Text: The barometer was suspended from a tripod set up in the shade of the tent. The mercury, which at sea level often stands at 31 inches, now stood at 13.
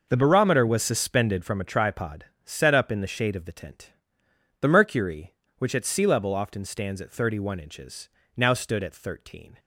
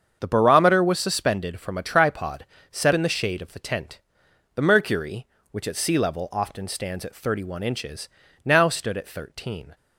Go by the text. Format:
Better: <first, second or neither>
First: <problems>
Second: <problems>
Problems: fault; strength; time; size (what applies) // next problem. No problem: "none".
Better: first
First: pauses between "tripod" and "set"; slight; at 2.2 s; 0.20 s long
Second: starts louder than the rest; strong; until 1.2 s; 7 dB // pauses between "tripod" and "set"; slight; at 2.4 s; 0.26 s long // skips "up"; at 2.9 s